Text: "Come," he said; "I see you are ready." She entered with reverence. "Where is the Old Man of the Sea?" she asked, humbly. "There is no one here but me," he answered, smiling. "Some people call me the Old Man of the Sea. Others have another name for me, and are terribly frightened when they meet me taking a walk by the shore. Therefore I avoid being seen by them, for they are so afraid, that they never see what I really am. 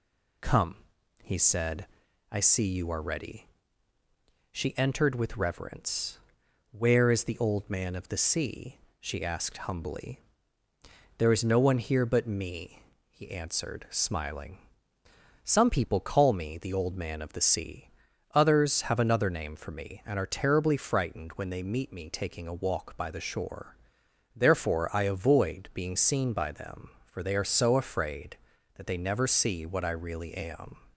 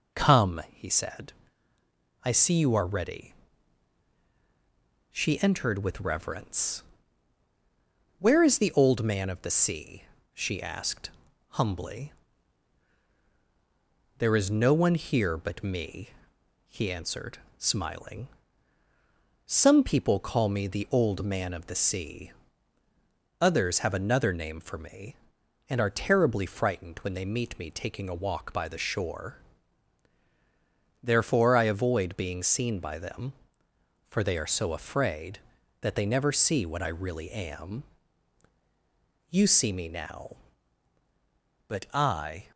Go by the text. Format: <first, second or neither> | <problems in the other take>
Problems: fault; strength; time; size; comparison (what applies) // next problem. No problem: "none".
first | goes on to say "You see me now But I"; strong; from 39.2 s on; 3.2 s long